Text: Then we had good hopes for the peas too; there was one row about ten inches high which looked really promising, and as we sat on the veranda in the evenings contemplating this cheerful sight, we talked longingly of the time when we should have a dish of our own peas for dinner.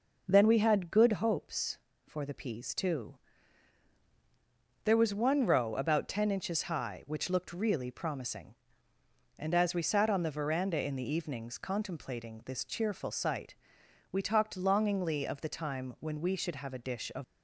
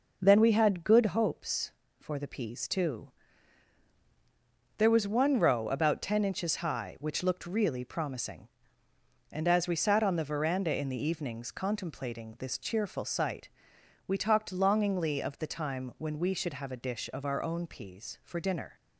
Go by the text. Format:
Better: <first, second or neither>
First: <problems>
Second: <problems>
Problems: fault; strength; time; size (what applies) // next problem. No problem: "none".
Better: second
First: stops before "our own peas for dinner"; at 17.2 s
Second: none